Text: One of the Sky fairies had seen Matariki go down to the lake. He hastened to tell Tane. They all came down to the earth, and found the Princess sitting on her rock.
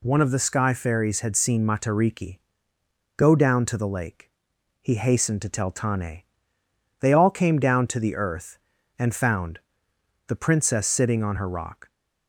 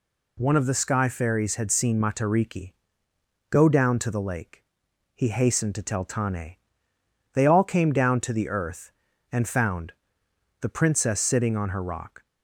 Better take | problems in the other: neither | pauses between "Matariki" and "go"; noticeable; the same in both // pauses between "found" and "the"; noticeable; the same in both

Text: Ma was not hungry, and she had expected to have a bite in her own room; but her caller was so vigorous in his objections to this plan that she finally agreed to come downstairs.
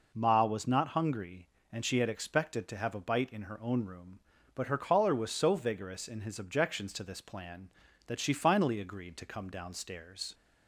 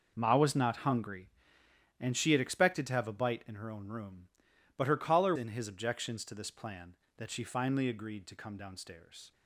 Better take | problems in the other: first | skips "was so vigorous"; at 5.3 s

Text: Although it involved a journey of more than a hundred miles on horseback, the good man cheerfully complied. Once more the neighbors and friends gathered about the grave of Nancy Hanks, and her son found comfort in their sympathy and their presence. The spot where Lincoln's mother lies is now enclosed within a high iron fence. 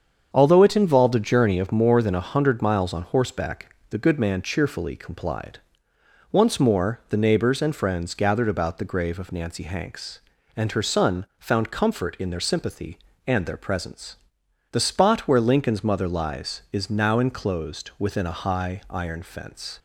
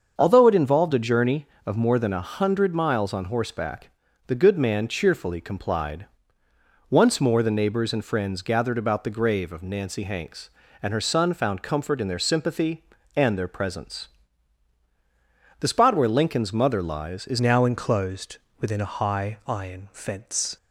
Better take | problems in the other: first | starts louder than the rest; until 1.1 s; 6.5 dB; strong in the first // changes voice at "now"; from 17.4 s on; 3.1 s long // pauses between "enclosed" and "within"; slight; at 18.3 s; 0.24 s long

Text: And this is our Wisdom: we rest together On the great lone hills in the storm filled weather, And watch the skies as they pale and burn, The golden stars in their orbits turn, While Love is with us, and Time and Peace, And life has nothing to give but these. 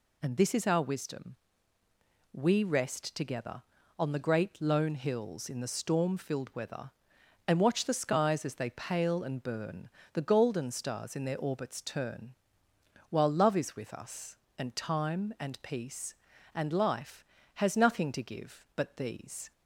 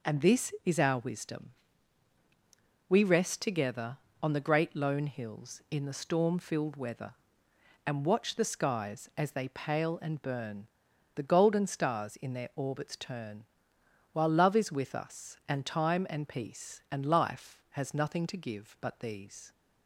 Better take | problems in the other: neither | none

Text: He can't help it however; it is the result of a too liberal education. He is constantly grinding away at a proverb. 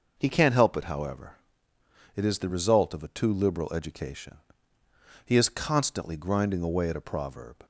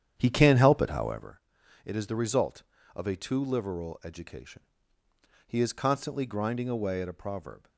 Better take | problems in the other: first | starts louder than the rest; strong; until 1.4 s; 9.5 dB

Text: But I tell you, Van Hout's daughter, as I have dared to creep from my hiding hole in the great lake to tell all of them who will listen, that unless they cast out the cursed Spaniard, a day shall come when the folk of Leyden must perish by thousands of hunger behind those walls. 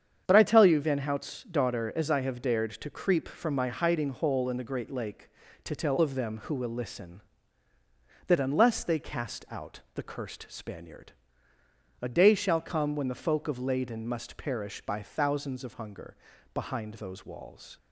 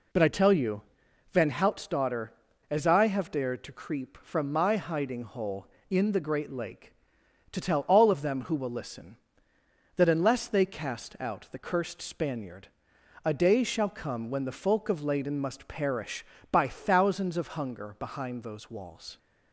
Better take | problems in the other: second | starts louder than the rest; strong; until 1.2 s; 8 dB // skips "all"; at 5.9 s // pauses between "hunger" and "behind"; at 16.1 s; 0.38 s long

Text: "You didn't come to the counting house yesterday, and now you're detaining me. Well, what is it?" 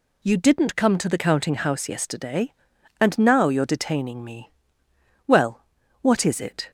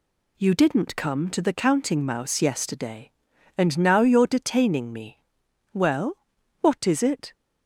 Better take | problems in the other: first | says "mouse" for "house"; at 2.0 s

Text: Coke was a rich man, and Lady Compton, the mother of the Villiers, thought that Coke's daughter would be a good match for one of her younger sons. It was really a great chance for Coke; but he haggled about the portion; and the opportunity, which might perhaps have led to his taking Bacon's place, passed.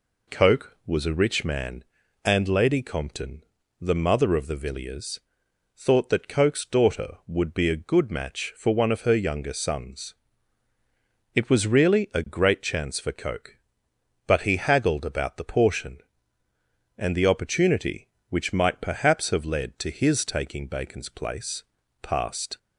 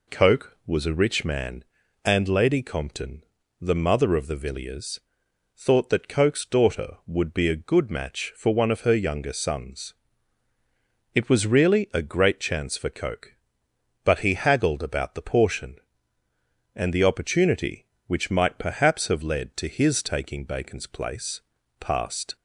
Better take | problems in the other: neither | none

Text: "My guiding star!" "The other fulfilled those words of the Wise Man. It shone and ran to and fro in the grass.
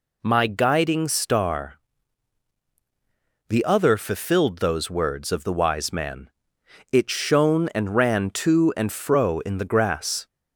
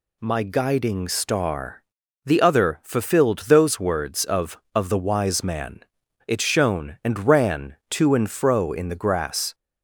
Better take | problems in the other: first | says "of" twice; at 4.7 s

